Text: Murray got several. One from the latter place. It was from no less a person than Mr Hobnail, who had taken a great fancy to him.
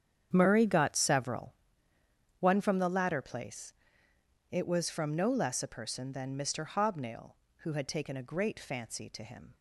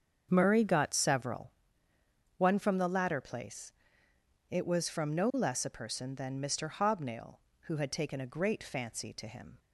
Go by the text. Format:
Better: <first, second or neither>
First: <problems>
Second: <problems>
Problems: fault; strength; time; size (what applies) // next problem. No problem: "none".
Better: second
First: gets quieter; strong; throughout; 15.5 dB // starts louder than the rest; strong; until 1.3 s; 8.5 dB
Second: starts louder than the rest; strong; until 1.3 s; 7 dB